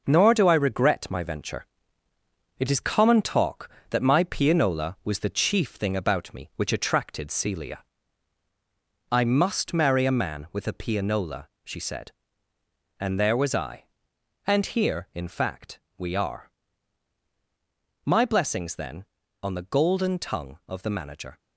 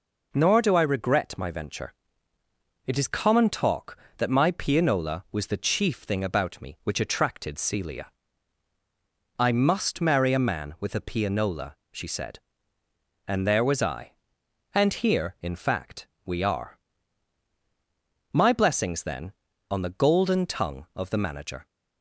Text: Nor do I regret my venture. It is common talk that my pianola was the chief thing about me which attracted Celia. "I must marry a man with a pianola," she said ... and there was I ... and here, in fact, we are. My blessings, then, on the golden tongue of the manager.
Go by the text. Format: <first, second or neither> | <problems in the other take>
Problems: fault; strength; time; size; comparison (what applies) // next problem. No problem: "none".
second | gets quieter; noticeable; throughout; 6 dB